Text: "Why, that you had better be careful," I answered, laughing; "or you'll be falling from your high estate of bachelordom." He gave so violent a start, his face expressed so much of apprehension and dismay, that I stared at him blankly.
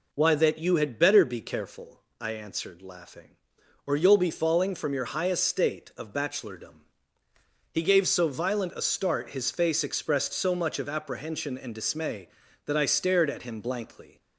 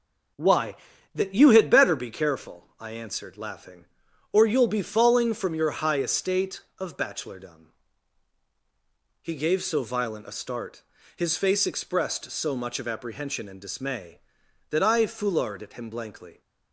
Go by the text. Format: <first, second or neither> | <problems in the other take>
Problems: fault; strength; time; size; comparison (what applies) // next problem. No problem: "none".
first | says "foulard" for "stared"; at 15.0 s